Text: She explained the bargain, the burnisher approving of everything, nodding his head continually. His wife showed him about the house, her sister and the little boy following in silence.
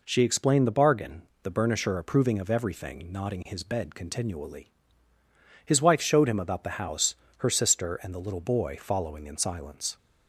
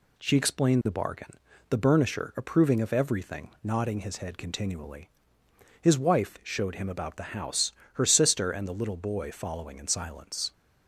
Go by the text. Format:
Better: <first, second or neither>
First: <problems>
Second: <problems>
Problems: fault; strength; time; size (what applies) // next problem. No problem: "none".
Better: second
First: says "bed" for "head"; at 3.6 s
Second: none